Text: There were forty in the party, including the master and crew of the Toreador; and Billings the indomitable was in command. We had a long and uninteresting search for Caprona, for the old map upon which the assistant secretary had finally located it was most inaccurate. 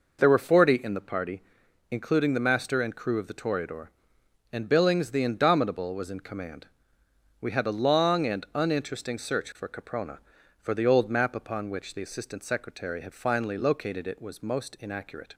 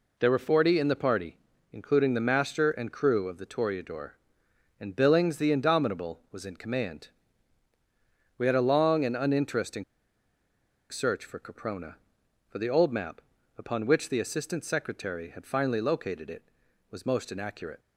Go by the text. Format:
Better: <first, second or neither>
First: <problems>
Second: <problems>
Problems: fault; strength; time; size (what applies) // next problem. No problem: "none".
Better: first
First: none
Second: pauses between "uninteresting" and "search"; at 9.8 s; 1.0 s long // pauses between "map" and "upon"; slight; at 13.2 s; 0.36 s long